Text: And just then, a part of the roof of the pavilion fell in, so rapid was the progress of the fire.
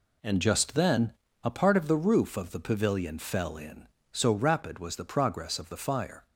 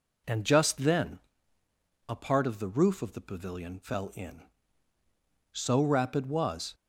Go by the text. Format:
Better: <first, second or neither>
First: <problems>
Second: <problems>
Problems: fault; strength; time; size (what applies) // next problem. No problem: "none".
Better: first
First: none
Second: stops before "the progress of the fire"; at 6.7 s